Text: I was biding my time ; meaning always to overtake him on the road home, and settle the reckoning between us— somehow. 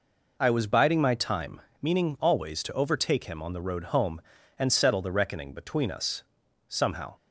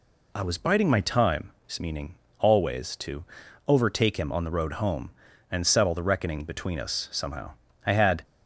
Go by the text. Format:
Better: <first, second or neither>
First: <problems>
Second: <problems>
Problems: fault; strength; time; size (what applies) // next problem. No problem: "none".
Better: first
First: none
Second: pauses between "meaning" and "always"; slight; at 2.1 s; 0.24 s long // pauses between "to" and "overtake"; at 3.2 s; 0.42 s long // goes on to say "I had"; slight; from 7.8 s on; 0.38 s long